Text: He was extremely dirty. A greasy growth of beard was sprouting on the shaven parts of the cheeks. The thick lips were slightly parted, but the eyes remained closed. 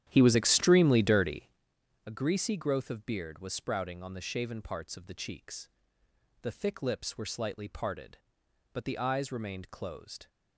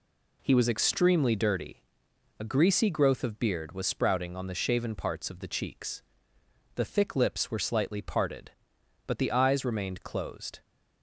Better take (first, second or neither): second